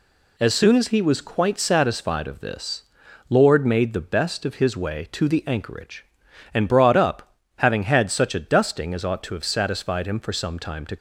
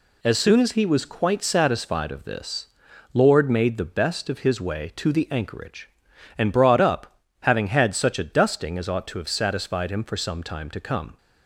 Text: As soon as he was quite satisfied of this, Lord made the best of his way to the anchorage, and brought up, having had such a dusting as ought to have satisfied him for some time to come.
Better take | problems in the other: second | stops before "come"; at 10.9 s

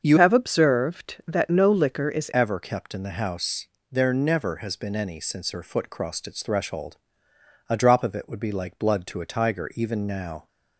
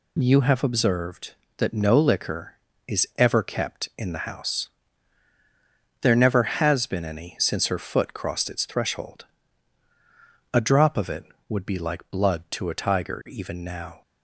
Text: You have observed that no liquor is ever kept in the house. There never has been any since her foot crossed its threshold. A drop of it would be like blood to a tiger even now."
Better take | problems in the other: second | starts louder than the rest; until 1.0 s; 7 dB // changes voice from "have" to "is"; from 0.1 to 2.2 s; 2.1 s long

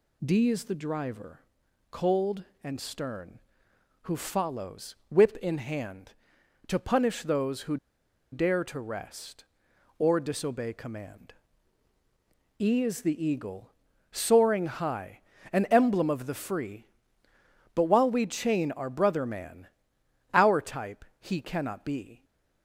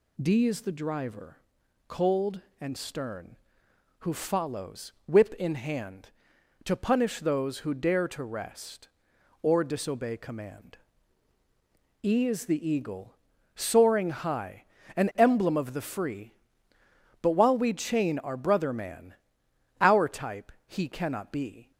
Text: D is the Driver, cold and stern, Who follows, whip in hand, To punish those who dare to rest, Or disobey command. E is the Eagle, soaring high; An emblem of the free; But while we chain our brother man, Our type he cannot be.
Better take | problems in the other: second | pauses between "who" and "dare"; noticeable; at 7.7 s; 0.55 s long // pauses between "type" and "he"; slight; at 21.0 s; 0.16 s long; slight in the second

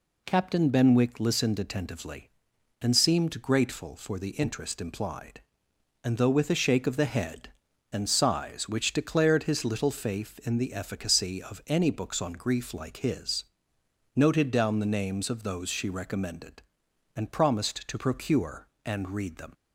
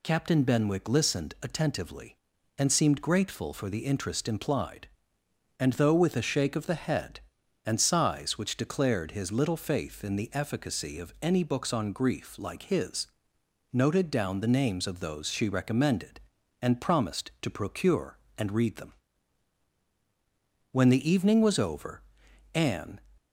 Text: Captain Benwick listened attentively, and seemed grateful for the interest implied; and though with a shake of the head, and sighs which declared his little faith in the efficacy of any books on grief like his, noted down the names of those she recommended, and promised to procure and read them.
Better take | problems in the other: first | goes on to say "When the evening was over Anne"; strong; from 20.7 s on; 2.3 s long

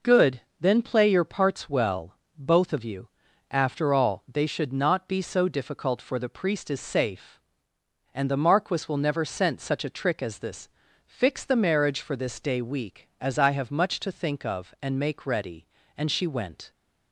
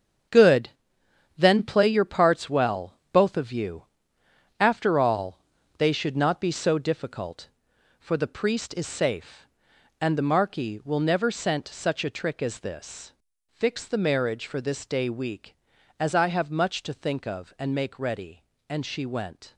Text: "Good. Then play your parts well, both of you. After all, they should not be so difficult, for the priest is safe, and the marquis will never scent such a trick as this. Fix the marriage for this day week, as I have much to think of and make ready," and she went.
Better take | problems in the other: first | gets quieter; strong; throughout; 10 dB

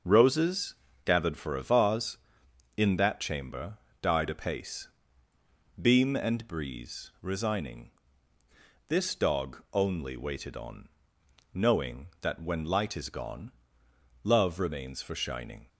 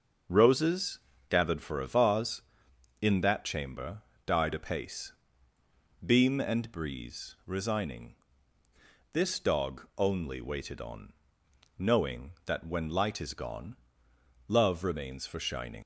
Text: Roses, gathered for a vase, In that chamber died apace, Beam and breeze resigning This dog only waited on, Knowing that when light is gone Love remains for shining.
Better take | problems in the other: first | starts louder than the rest; until 1.5 s; 6.5 dB; also in the first // pauses between "chamber" and "died"; slight; at 4.0 s; 0.24 s long; slight in the first // pauses between "resigning" and "This"; noticeable; at 8.1 s; 0.98 s long; noticeable in the first // pauses between "gone" and "Love"; noticeable; at 13.7 s; 0.72 s long; noticeable in the first // leaves "shining" unfinished; at 15.8 s; 100 ms

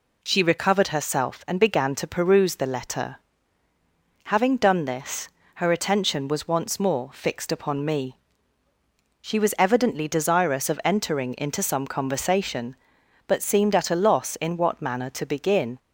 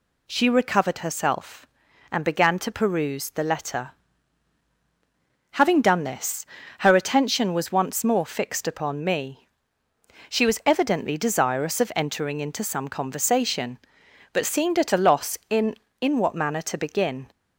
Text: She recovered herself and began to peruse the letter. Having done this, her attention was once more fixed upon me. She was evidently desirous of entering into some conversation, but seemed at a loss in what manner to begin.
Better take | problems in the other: first | says "in" twice; at 16.0 s

